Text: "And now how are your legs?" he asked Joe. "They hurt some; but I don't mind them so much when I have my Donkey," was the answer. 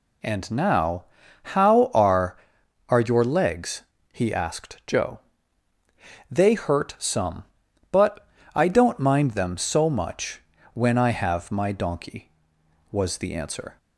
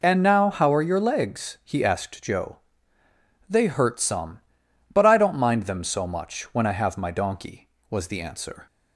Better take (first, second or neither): second